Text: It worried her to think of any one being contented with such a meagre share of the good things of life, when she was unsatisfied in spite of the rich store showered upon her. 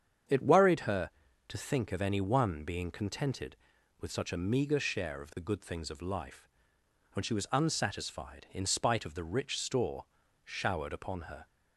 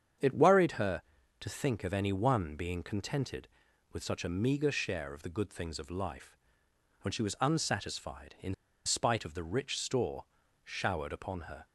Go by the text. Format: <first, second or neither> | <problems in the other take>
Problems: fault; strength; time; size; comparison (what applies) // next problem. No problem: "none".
first | starts louder than the rest; strong; until 1.5 s; 7.5 dB; strong in the first // pauses between "in" and "spite"; slight; at 8.5 s; 0.32 s long // pauses between "store" and "showered"; at 10.2 s; 0.40 s long; also in the first